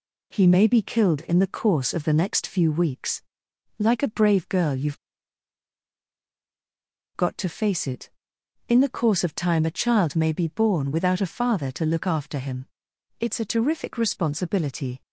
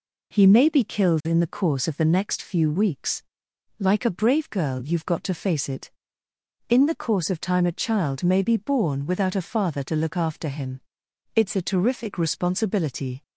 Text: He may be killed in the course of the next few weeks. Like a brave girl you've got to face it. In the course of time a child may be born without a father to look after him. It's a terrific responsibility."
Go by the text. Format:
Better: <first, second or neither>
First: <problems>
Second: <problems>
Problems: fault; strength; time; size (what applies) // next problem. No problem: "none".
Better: second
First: pauses between "you've" and "got"; strong; at 4.9 s; 2.1 s long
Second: none